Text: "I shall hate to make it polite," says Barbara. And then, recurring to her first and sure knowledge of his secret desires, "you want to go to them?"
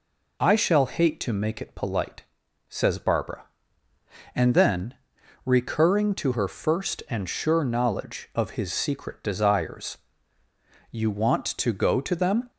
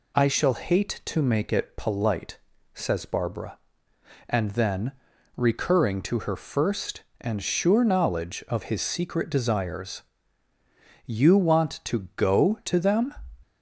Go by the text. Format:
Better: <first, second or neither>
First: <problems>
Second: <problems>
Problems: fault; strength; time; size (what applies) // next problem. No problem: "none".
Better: neither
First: none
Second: none